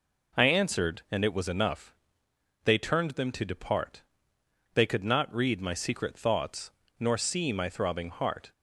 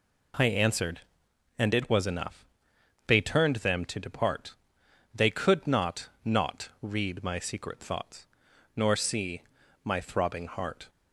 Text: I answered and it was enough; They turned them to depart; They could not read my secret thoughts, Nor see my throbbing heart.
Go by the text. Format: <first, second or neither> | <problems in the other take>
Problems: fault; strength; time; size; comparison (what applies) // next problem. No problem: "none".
first | says "not" twice; at 6.2 s // pauses between "see" and "my"; at 9.4 s; 0.42 s long